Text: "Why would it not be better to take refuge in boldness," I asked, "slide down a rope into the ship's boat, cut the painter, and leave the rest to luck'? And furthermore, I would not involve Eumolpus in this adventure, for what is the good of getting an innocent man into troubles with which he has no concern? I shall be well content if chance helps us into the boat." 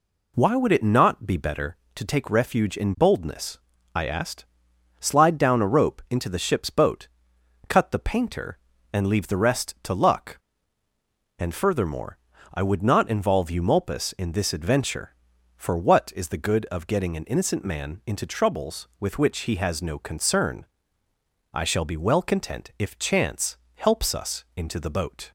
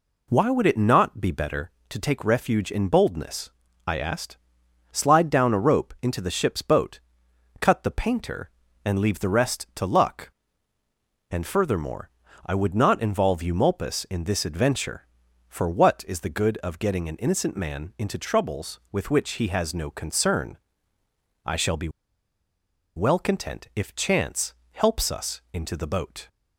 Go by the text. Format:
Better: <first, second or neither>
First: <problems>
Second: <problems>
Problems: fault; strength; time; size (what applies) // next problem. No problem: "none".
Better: first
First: pauses between "chance" and "helps"; slight; at 23.5 s; 0.16 s long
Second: pauses between "be" and "well"; at 21.8 s; 1.0 s long // pauses between "chance" and "helps"; slight; at 24.5 s; 0.16 s long